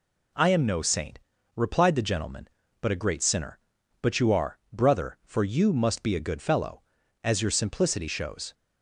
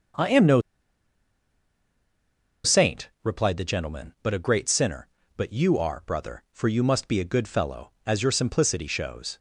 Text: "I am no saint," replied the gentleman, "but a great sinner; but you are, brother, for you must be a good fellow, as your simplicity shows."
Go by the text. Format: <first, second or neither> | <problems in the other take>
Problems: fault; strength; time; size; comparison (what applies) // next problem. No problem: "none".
first | starts louder than the rest; until 3.3 s; 6.5 dB // pauses between "no" and "saint"; strong; at 0.6 s; 2.0 s long